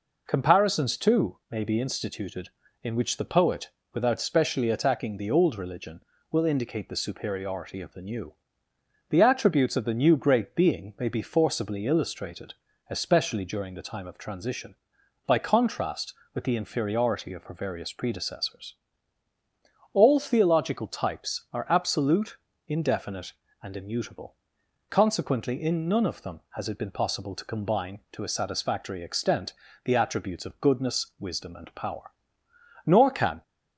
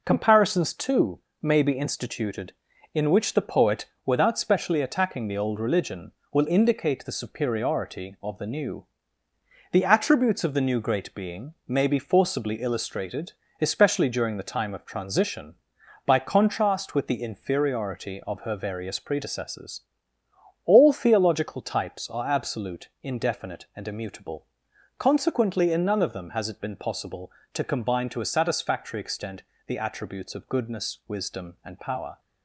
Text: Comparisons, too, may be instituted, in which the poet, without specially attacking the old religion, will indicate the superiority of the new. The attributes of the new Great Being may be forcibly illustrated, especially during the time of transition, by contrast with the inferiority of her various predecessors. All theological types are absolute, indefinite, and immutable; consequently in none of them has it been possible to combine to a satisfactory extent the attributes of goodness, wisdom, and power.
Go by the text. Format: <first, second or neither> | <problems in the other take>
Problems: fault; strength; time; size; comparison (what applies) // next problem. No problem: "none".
second | pauses between "extent" and "the"; slight; at 29.5 s; 0.32 s long; slight in the second // goes on to say "Nor can"; from 32.8 s on; 0.56 s long